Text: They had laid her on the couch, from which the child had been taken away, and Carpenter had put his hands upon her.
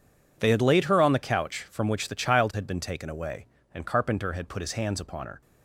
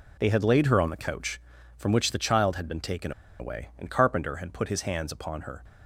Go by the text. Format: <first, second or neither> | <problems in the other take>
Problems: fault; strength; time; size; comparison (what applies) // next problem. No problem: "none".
first | pauses between "taken" and "away"; slight; at 3.1 s; 0.28 s long